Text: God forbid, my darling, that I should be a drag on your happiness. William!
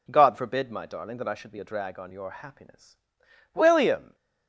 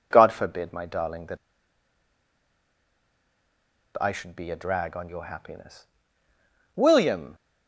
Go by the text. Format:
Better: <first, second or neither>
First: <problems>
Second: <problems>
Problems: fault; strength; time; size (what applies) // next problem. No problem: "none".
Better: first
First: none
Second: pauses between "that" and "I"; strong; at 1.3 s; 2.6 s long